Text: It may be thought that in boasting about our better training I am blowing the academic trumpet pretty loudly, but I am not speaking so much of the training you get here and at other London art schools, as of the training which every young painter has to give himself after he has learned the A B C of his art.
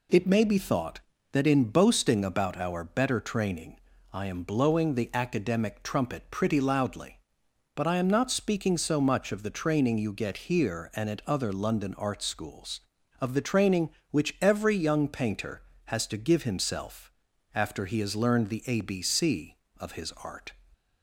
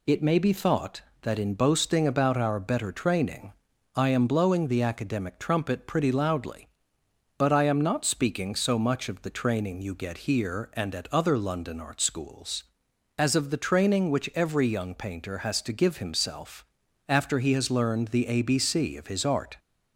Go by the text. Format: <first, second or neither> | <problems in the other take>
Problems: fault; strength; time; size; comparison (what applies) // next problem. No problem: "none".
second | pauses between "training" and "I"; slight; at 3.7 s; 0.34 s long; also in the second // skips "as"; at 13.0 s // pauses between "himself" and "after"; at 17.1 s; 0.42 s long; also in the second